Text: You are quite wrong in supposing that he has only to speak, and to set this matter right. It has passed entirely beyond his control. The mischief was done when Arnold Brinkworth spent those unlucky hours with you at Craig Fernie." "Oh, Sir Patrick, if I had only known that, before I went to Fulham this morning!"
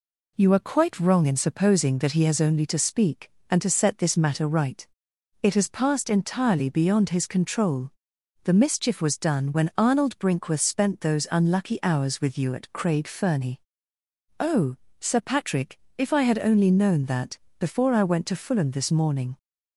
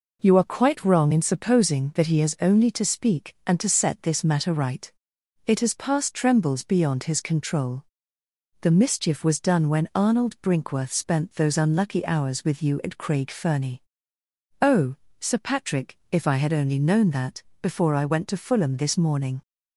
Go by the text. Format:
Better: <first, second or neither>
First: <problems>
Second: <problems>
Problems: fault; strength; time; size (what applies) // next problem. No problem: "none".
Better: first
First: none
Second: says "trembles" for "entirely"; at 6.1 s